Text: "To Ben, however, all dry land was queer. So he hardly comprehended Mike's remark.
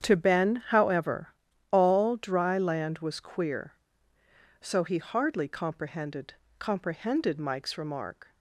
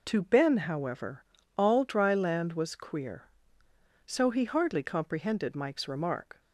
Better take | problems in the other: second | starts louder than the rest; strong; until 1.0 s; 8.5 dB // says "comprehended" twice; at 6.5 s

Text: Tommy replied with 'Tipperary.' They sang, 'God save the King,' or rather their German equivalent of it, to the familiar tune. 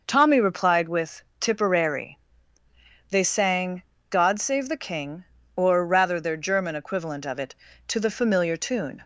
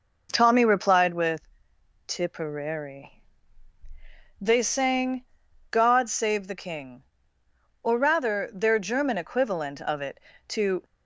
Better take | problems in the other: first | pauses between "with" and "Tipperary"; noticeable; at 1.4 s; 0.66 s long; slight in the first // stops before "the familiar tune"; at 10.8 s

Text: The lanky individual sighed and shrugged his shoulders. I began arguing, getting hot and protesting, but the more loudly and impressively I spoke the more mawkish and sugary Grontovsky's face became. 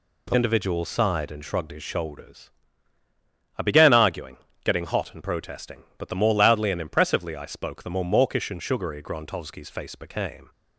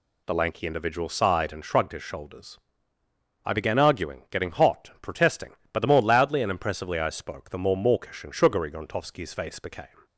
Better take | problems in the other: second | skips "lanky"; at 0.3 s

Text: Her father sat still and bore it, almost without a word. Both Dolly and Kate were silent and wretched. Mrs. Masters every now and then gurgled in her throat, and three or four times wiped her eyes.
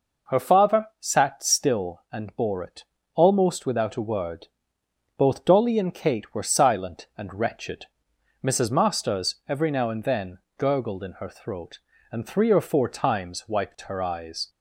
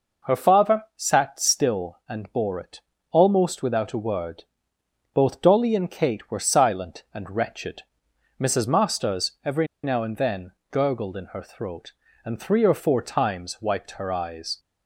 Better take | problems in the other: first | pauses between "every" and "now"; slight; at 9.6 s; 0.17 s long // pauses between "then" and "gurgled"; slight; at 10.5 s; 0.20 s long; slight in the first

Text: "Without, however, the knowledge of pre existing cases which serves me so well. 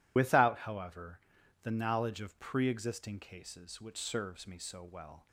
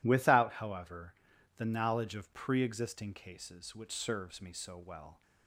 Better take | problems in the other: second | loses the start of "Without"; at 0.1 s; 65 ms

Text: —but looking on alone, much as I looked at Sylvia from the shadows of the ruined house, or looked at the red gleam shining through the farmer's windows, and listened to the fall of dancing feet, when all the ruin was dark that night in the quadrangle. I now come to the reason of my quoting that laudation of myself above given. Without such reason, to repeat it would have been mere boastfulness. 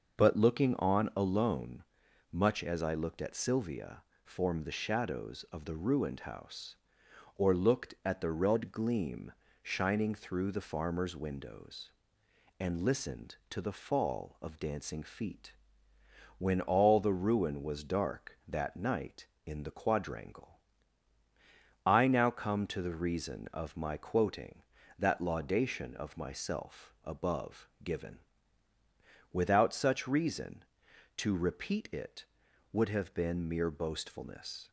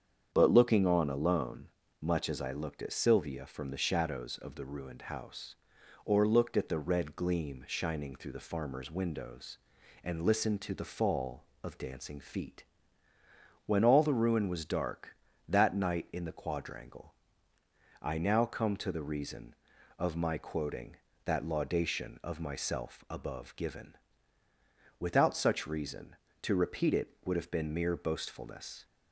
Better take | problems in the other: second | starts louder than the rest; noticeable; until 1.2 s; 6 dB; strong in the second // says "form" for "from"; at 4.2 s // pauses between "gleam" and "shining"; slight; at 9.3 s; 0.30 s long // pauses between "above" and "given"; slight; at 27.6 s; 0.16 s long

